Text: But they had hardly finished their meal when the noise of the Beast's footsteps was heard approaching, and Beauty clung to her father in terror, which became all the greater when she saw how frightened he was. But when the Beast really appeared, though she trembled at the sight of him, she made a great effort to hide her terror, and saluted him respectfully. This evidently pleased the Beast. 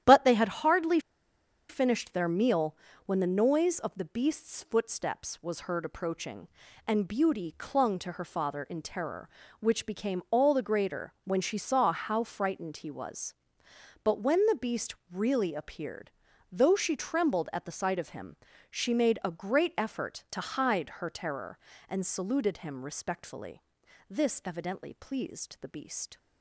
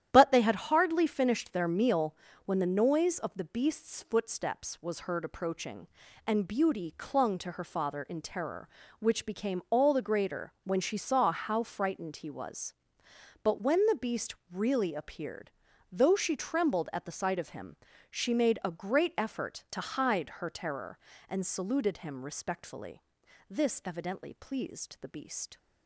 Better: second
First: starts louder than the rest; strong; until 1.7 s; 11 dB // pauses between "hardly" and "finished"; noticeable; at 0.9 s; 0.69 s long // pauses between "meal" and "when"; slight; at 2.7 s; 0.30 s long // pauses between "Beast" and "really"; slight; at 14.9 s; 0.16 s long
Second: starts louder than the rest; strong; until 1.1 s; 11 dB // pauses between "meal" and "when"; slight; at 2.1 s; 0.30 s long // pauses between "Beast" and "really"; slight; at 14.3 s; 0.16 s long

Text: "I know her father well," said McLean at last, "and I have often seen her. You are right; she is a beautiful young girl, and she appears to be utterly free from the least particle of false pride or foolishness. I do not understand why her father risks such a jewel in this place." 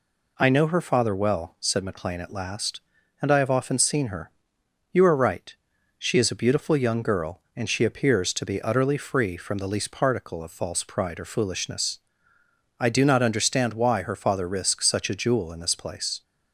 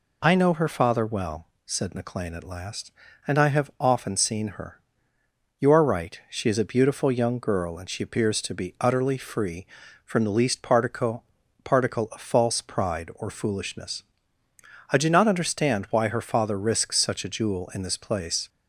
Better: first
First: none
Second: says "particle" twice; at 11.6 s

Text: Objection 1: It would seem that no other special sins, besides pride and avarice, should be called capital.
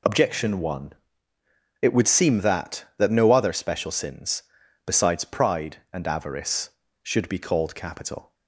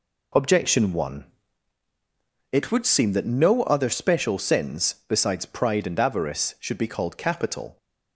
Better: second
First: says "that" twice; at 2.9 s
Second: none

